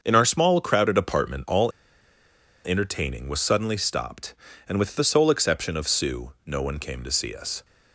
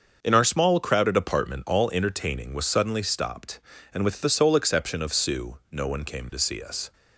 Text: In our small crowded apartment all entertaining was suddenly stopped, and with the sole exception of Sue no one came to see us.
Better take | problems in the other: second | starts louder than the rest; until 1.0 s; 6.5 dB; also in the second // pauses between "all" and "entertaining"; noticeable; at 1.7 s; 0.95 s long

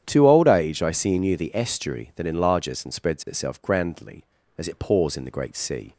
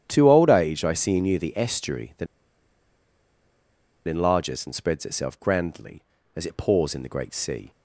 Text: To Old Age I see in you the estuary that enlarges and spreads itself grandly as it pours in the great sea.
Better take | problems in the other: first | starts louder than the rest; strong; until 1.0 s; 9.5 dB; strong in the first // pauses between "that" and "enlarges"; strong; at 2.2 s; 1.8 s long

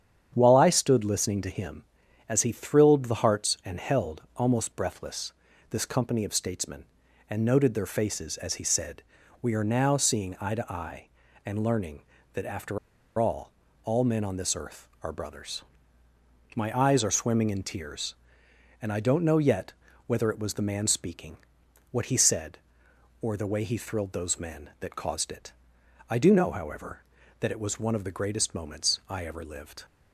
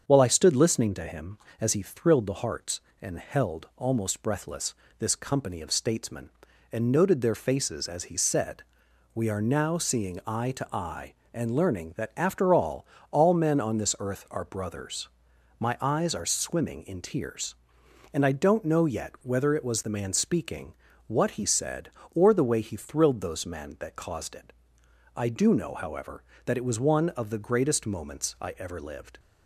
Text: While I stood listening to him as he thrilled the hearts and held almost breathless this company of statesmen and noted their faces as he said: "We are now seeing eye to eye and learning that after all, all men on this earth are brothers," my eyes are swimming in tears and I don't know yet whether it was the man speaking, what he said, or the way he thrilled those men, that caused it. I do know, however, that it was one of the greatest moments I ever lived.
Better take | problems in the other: second | starts louder than the rest; strong; until 1.3 s; 8.5 dB; strong in the second // pauses between "breathless" and "this"; at 5.3 s; 0.38 s long; slight in the second // pauses between "after" and "all"; at 12.7 s; 0.40 s long // pauses between "yet" and "whether"; slight; at 19.7 s; 0.34 s long

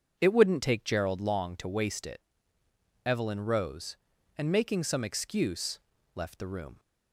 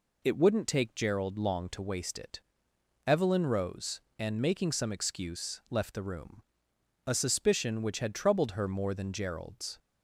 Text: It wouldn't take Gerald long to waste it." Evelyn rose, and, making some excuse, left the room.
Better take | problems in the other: first | goes on to say "A suspicion which had troubled her more than Gerald's"; strong; from 7.0 s on; 2.7 s long

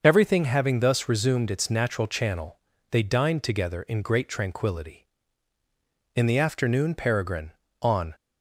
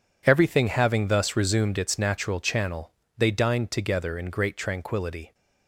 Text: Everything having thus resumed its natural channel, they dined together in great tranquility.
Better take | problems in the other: second | starts louder than the rest; until 1.0 s; 6.5 dB // goes on to say "In the afternoon Peregrine on"; strong; from 6.1 s on; 2.0 s long

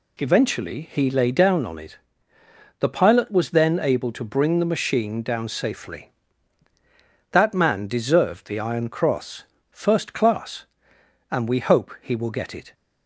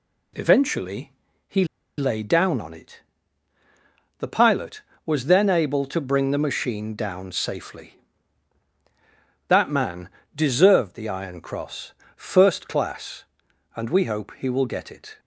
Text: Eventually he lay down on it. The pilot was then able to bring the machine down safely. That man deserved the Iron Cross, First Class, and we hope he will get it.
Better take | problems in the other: first | pauses between "Eventually" and "he"; slight; at 1.1 s; 0.36 s long // pauses between "he" and "lay"; slight; at 1.6 s; 0.33 s long // pauses between "man" and "deserved"; slight; at 10.0 s; 0.26 s long

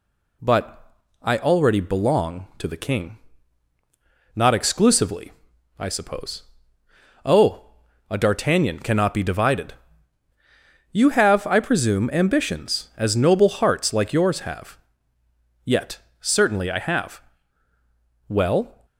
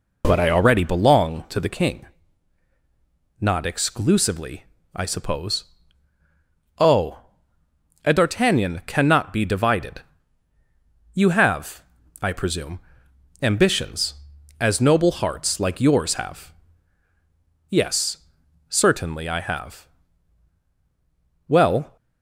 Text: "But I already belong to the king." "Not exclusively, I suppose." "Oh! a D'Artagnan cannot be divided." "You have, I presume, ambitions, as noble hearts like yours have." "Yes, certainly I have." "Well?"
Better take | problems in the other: second | pauses between "But" and "I"; slight; at 0.9 s; 0.28 s long // says "Yet" for "Yes"; at 15.6 s

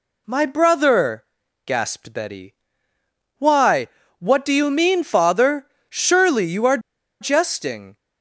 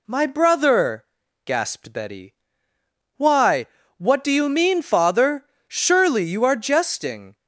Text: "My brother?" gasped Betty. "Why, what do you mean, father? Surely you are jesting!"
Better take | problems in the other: second | pauses between "are" and "jesting"; at 6.7 s; 0.42 s long

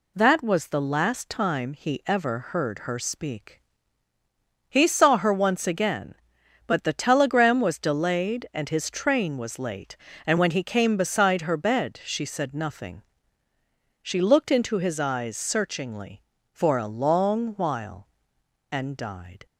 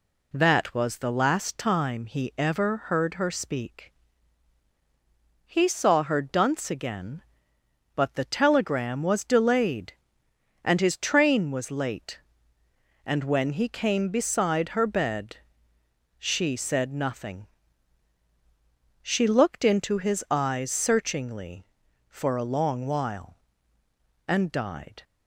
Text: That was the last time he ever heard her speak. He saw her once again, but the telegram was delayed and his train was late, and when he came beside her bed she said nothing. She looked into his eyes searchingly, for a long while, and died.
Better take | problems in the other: first | says "dunce" for "once"; at 6.2 s // pauses between "bed" and "she"; noticeable; at 15.3 s; 0.82 s long

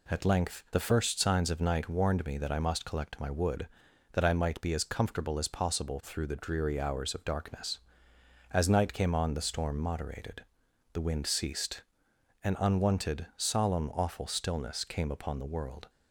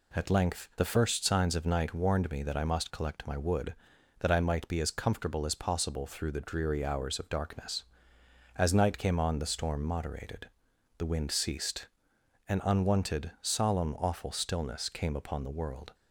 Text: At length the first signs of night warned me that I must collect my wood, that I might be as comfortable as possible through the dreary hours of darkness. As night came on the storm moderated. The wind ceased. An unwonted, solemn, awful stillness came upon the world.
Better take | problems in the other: neither | none

